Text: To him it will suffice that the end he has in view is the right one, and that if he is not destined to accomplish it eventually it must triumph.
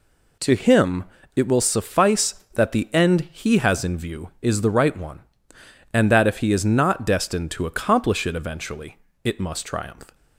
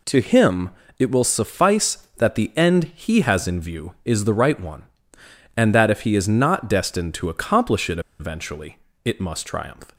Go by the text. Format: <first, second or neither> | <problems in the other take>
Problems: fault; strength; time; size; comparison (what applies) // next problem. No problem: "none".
first | pauses between "him" and "it"; slight; at 0.6 s; 0.28 s long; slight in the first // pauses between "it" and "eventually"; slight; at 7.9 s; 0.19 s long // pauses between "eventually" and "it"; slight; at 8.7 s; 0.28 s long; slight in the first